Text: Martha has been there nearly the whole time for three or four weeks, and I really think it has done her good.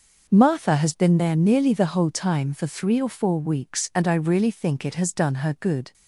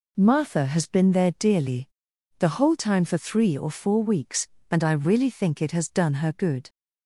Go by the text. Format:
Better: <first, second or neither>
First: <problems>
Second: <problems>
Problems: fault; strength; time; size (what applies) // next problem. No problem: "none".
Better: first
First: none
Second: says "dearly" for "nearly"; at 1.3 s